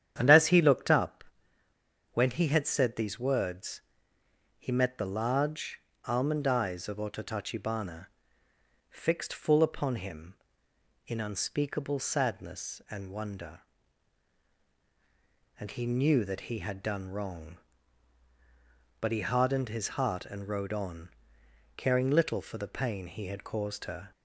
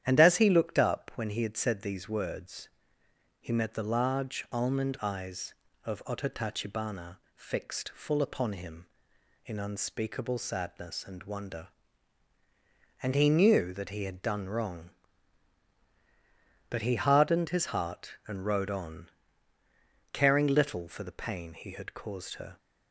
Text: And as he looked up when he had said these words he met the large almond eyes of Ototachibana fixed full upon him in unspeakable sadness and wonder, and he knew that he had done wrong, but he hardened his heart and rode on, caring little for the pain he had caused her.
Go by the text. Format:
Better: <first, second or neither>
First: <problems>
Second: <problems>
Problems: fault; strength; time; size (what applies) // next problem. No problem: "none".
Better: second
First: starts louder than the rest; strong; until 1.1 s; 9 dB // pauses between "up" and "when"; noticeable; at 1.2 s; 0.90 s long // pauses between "words" and "he"; noticeable; at 3.8 s; 0.76 s long // pauses between "large" and "almond"; slight; at 5.8 s; 0.24 s long // pauses between "Ototachibana" and "fixed"; noticeable; at 8.0 s; 0.82 s long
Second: starts louder than the rest; strong; until 1.0 s; 10.5 dB // pauses between "words" and "he"; noticeable; at 2.6 s; 0.70 s long // pauses between "Ototachibana" and "fixed"; slight; at 7.1 s; 0.16 s long